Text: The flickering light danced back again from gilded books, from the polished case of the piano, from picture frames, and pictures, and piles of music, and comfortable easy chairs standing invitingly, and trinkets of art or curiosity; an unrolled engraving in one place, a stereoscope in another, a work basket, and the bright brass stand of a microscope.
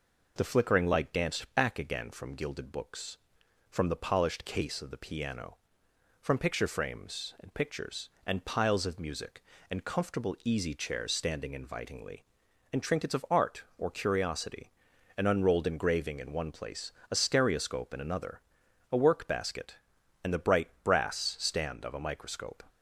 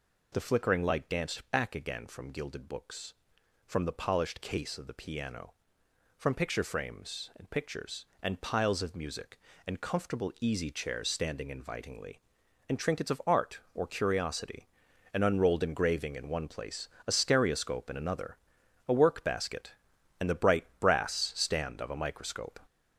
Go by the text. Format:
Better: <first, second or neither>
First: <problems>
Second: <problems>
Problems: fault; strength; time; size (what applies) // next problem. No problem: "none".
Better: first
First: none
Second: gets louder; noticeable; throughout; 6 dB